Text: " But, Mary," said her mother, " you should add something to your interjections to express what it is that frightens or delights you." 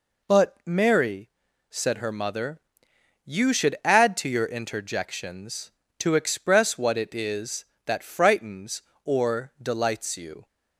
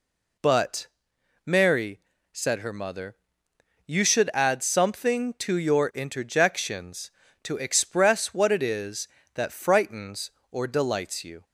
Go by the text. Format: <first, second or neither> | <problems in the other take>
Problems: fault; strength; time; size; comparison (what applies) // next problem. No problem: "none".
second | skips "something"; at 4.1 s